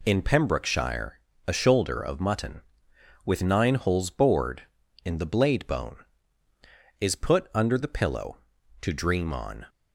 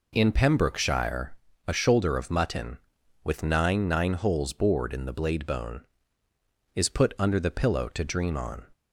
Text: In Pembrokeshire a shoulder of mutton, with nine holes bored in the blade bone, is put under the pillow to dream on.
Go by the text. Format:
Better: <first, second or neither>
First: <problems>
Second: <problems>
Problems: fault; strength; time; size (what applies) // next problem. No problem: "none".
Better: first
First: pauses between "Pembrokeshire" and "a"; slight; at 1.1 s; 0.26 s long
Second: pauses between "Pembrokeshire" and "a"; slight; at 1.3 s; 0.34 s long // says "nine" twice; at 3.8 s